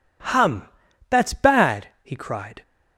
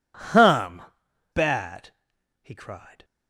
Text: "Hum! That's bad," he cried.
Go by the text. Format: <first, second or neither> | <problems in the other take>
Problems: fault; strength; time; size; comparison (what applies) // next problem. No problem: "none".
first | skips "That's"; at 1.0 s